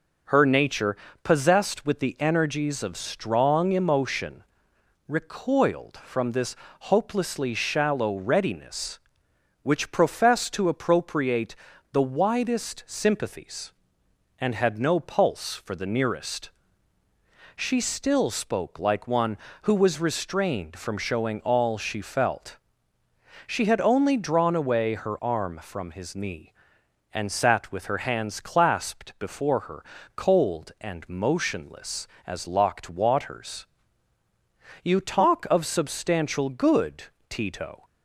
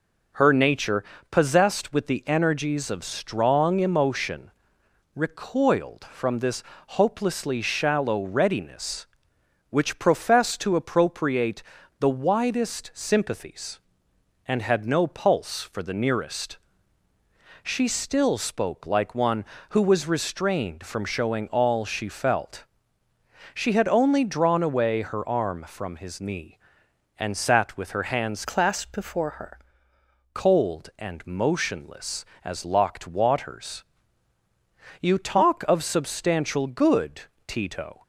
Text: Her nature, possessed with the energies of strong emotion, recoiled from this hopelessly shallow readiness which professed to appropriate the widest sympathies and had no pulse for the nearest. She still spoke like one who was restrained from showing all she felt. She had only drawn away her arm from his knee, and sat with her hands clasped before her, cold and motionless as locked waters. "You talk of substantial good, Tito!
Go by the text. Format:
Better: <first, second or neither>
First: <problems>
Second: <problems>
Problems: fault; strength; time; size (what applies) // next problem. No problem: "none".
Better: first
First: pauses between "this" and "hopelessly"; slight; at 6.5 s; 0.24 s long // pauses between "appropriate" and "the"; at 11.5 s; 0.38 s long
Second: pauses between "this" and "hopelessly"; slight; at 6.6 s; 0.24 s long // pauses between "appropriate" and "the"; at 11.6 s; 0.38 s long // changes voice from "clasped" to "her"; from 28.4 to 29.5 s; 1.1 s long